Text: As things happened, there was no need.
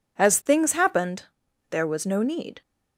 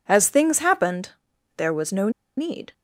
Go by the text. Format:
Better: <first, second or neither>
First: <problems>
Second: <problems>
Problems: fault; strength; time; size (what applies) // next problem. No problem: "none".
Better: first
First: none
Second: pauses between "no" and "need"; slight; at 2.0 s; 0.27 s long